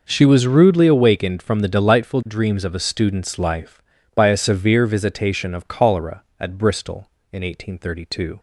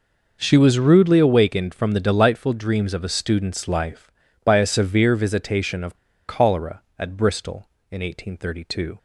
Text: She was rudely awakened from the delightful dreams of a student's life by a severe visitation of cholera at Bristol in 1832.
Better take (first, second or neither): first